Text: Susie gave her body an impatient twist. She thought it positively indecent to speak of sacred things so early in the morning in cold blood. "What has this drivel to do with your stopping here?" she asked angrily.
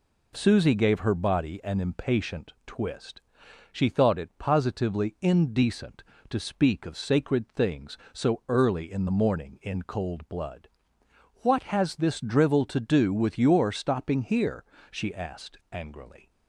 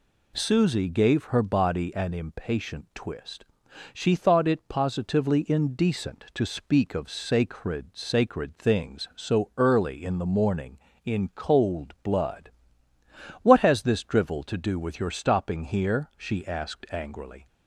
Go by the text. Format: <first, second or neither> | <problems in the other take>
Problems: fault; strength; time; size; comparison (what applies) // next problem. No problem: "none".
first | says "sacred" twice; at 7.9 s